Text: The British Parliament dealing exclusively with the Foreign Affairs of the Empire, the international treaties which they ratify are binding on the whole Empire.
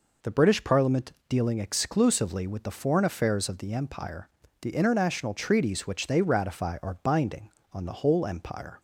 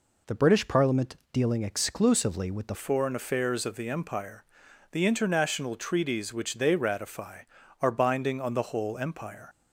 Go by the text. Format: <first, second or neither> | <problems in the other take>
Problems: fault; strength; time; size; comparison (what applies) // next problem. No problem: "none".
first | pauses between "Parliament" and "dealing"; slight; at 1.1 s; 0.16 s long; slight in the first // changes voice at "Foreign"; from 2.7 s on; 6.7 s long